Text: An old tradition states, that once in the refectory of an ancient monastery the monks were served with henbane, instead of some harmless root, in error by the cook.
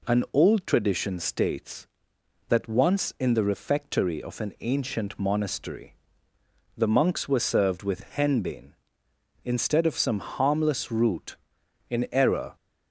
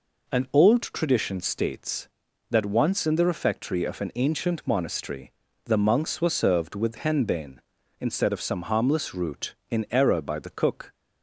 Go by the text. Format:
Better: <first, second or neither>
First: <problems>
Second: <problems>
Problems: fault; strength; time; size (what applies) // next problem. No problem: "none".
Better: second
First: pauses between "monastery" and "the"; noticeable; at 5.9 s; 0.80 s long // stops before "by the cook"; at 12.5 s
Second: pauses between "monastery" and "the"; slight; at 5.3 s; 0.34 s long